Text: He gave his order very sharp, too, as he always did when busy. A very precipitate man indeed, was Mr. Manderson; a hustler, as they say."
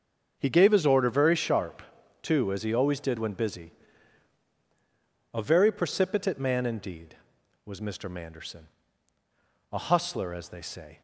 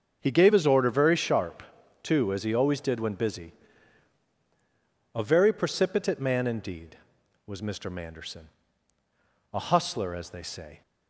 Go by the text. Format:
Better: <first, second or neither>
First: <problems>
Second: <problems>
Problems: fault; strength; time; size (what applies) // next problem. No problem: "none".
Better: neither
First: starts louder than the rest; until 1.3 s; 6.5 dB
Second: starts louder than the rest; until 1.2 s; 6.5 dB